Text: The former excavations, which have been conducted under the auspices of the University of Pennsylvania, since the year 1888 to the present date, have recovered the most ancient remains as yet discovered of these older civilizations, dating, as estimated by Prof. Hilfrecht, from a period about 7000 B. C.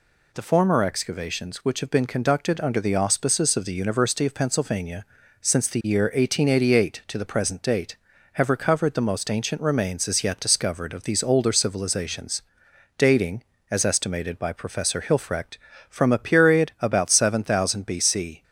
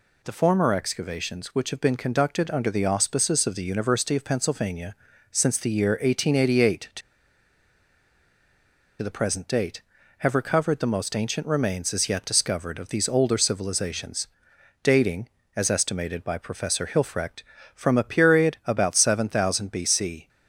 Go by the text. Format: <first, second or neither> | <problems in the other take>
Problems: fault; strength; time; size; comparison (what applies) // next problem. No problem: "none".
first | pauses between "to" and "the"; strong; at 7.0 s; 2.0 s long